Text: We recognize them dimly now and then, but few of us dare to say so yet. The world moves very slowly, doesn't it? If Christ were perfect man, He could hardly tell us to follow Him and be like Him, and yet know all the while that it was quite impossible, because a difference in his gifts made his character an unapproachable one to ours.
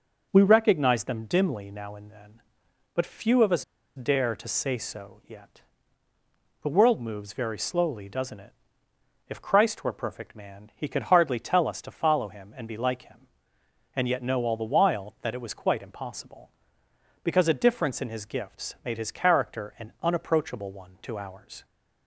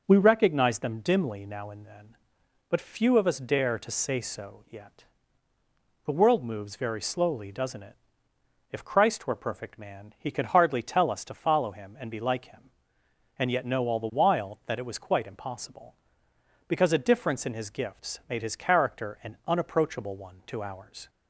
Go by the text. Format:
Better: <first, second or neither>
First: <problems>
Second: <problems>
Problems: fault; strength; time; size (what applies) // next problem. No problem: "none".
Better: second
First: pauses between "us" and "dare"; slight; at 3.6 s; 0.33 s long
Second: none